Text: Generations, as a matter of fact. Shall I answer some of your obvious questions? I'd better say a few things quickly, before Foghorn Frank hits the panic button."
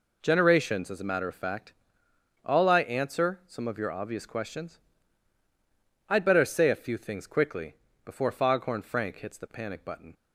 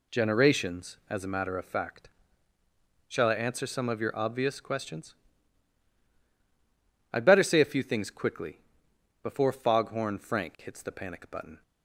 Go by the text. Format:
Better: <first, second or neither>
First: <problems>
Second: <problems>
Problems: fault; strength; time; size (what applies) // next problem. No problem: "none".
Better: second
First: says "All" for "Shall"; at 2.4 s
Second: none